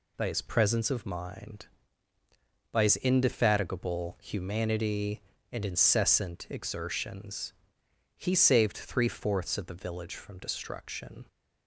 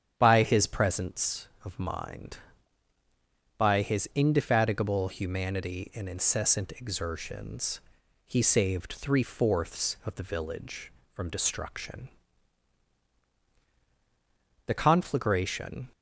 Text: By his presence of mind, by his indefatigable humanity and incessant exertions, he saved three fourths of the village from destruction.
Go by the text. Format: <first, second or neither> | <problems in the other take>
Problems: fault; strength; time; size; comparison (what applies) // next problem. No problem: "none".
first | starts louder than the rest; strong; until 1.1 s; 9 dB // goes on to say "The conflagration"; noticeable; from 14.6 s on; 1.2 s long